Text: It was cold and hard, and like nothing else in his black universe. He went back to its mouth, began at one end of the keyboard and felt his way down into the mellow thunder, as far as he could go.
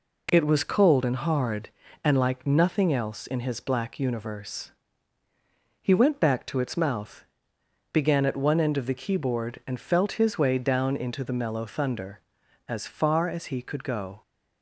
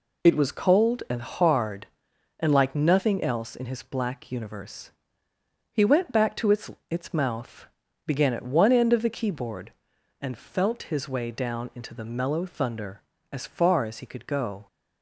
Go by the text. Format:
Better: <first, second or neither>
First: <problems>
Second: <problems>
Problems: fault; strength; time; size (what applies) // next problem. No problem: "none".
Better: first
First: none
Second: says "its" twice; at 6.9 s